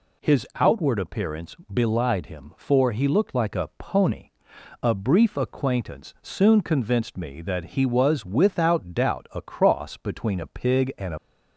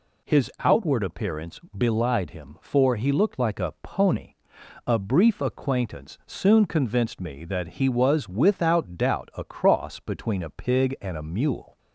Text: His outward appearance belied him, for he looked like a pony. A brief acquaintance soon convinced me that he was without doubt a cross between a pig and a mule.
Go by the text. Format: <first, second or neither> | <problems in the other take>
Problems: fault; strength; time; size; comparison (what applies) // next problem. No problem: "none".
second | pauses between "appearance" and "belied"; slight; at 1.5 s; 0.18 s long; slight in the second // stops before "mule"; at 11.1 s